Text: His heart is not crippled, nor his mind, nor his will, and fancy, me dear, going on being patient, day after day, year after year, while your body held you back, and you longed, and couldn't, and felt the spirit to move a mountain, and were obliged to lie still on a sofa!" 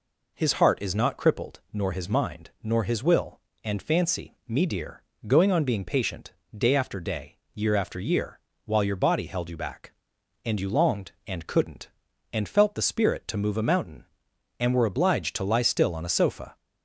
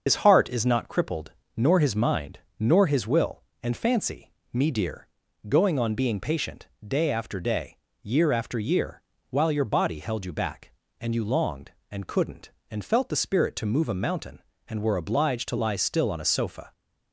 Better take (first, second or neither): first